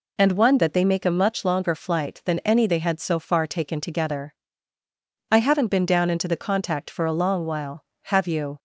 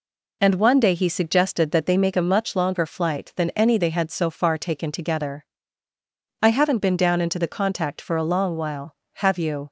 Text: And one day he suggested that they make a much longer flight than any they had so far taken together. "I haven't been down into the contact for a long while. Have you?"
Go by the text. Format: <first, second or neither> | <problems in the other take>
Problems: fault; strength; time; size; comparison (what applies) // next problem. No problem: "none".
second | skips "day he suggested"; at 0.5 s